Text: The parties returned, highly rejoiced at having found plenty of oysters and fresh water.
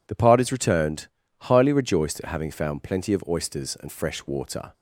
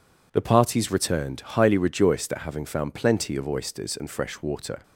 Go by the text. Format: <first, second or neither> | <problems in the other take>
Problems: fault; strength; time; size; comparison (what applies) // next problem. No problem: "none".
neither | none